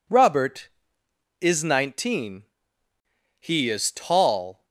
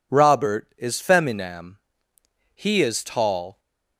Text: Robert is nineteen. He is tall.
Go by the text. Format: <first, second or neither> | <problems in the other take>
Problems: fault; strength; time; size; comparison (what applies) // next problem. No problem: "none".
first | says "feminam" for "nineteen"; at 1.0 s